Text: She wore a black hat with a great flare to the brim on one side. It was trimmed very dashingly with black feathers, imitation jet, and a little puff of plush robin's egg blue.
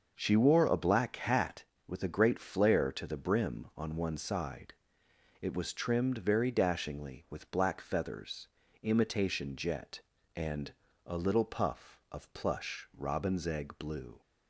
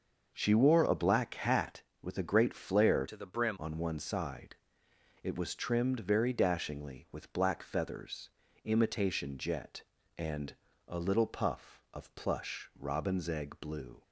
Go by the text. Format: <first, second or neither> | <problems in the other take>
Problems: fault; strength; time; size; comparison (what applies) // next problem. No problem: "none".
first | starts louder than the rest; until 1.3 s; 6 dB; also in the first // changes voice from "to" to "brim"; from 3.0 to 3.5 s; 0.5 s long // pauses between "and" and "a"; slight; at 10.5 s; 0.32 s long; slight in the first